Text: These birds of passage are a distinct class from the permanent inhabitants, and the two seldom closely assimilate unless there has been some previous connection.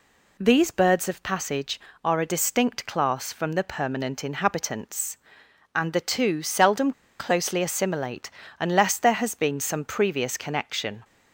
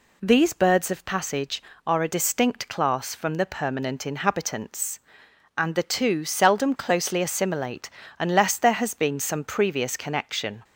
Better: second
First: pauses between "seldom" and "closely"; slight; at 6.9 s; 0.27 s long // pauses between "assimilate" and "unless"; slight; at 8.3 s; 0.30 s long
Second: pauses between "assimilate" and "unless"; slight; at 7.8 s; 0.30 s long

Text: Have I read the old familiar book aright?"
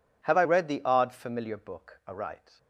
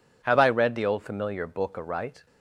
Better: second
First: says "odd" for "old"; at 0.8 s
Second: none

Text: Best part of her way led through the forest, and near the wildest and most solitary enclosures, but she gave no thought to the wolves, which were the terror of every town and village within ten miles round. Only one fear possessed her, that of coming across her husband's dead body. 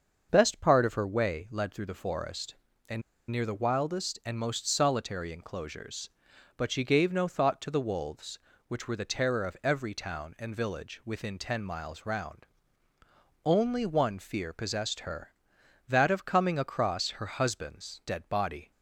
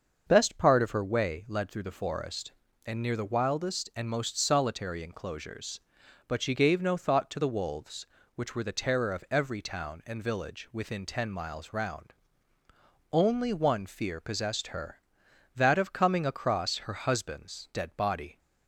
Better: second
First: starts louder than the rest; until 1.3 s; 6.5 dB // pauses between "and" and "near"; slight; at 3.0 s; 0.29 s long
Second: starts louder than the rest; until 1.2 s; 6.5 dB

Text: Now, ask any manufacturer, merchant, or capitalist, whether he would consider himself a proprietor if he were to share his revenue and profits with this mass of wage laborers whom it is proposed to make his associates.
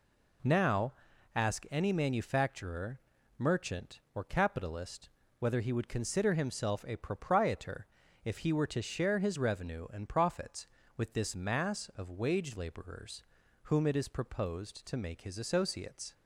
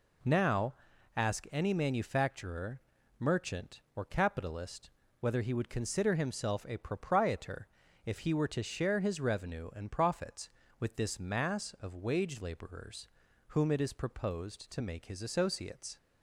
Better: neither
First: pauses between "proprietor" and "if"; at 7.8 s; 0.38 s long // pauses between "laborers" and "whom"; at 13.2 s; 0.40 s long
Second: pauses between "proprietor" and "if"; at 7.6 s; 0.38 s long // pauses between "laborers" and "whom"; at 13.0 s; 0.40 s long

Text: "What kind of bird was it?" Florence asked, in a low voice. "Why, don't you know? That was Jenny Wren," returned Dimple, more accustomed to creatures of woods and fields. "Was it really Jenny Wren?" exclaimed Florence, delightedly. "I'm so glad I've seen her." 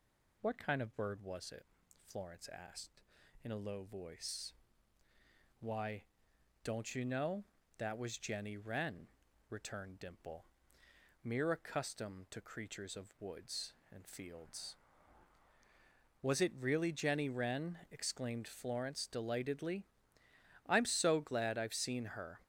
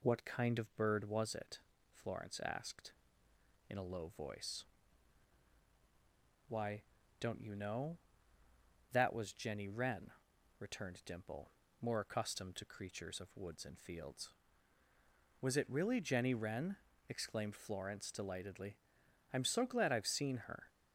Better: second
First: says "mere" for "more"; at 11.2 s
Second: none

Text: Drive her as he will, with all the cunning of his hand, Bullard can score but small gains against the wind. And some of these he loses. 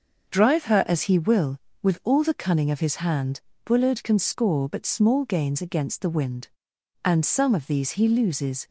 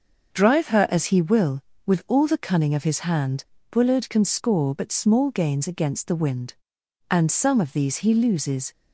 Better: neither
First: starts louder than the rest; until 1.3 s; 6.5 dB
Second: starts louder than the rest; until 1.3 s; 6.5 dB

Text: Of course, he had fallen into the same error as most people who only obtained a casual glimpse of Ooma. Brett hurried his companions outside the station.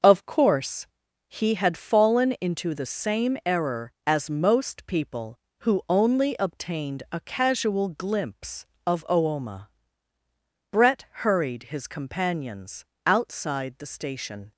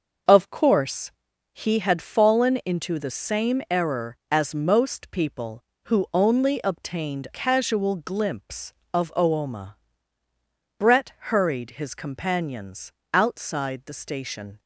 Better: first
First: pauses between "Brett" and "hurried"; slight; at 11.0 s; 0.20 s long // pauses between "companions" and "outside"; slight; at 12.8 s; 0.20 s long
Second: skips "a"; at 7.3 s // pauses between "Brett" and "hurried"; slight; at 11.1 s; 0.20 s long // pauses between "companions" and "outside"; slight; at 12.9 s; 0.20 s long

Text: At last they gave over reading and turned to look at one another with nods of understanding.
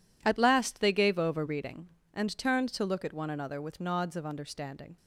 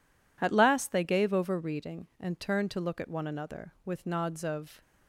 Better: first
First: none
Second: stops before "understanding"; at 4.8 s

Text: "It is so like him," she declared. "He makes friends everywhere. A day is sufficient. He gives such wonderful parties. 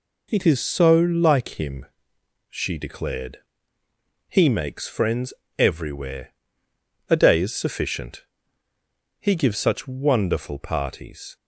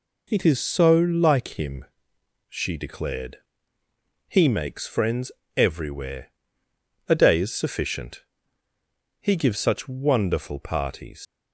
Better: first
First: pauses between "friends" and "everywhere"; slight; at 5.3 s; 0.26 s long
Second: pauses between "friends" and "everywhere"; slight; at 5.3 s; 0.26 s long // leaves "parties" unfinished; at 11.2 s; 115 ms

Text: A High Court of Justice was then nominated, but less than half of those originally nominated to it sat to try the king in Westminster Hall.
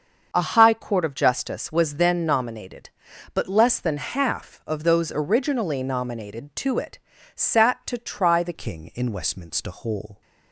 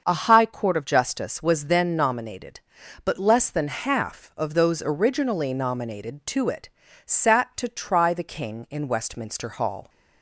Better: second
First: starts louder than the rest; until 1.3 s; 6.5 dB // pauses between "it" and "sat"; slight; at 6.9 s; 0.36 s long // changes voice at "king"; from 8.5 s on; 1.7 s long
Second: starts louder than the rest; until 1.0 s; 6.5 dB // pauses between "it" and "sat"; slight; at 6.6 s; 0.36 s long

